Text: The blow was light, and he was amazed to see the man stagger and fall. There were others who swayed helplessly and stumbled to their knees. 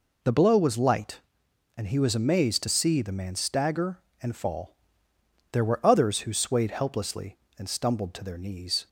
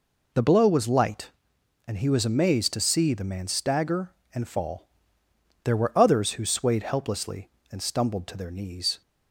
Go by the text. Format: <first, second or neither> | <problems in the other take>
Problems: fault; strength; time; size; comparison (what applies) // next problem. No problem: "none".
neither | none